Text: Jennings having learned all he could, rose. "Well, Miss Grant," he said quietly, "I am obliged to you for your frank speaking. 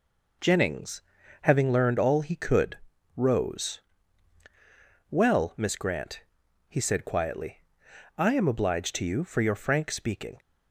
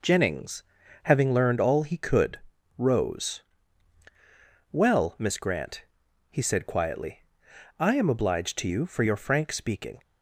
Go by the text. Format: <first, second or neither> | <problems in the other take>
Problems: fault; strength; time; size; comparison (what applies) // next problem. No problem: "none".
neither | pauses between "Jennings" and "having"; the same in both